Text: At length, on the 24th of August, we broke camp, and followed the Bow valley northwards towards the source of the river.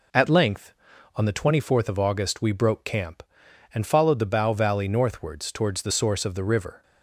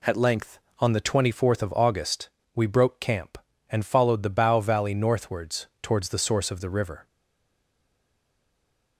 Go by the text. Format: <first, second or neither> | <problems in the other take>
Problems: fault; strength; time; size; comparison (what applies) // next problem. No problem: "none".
first | stays silent after the last word; noticeable; from 7.0 s on; 1.9 s long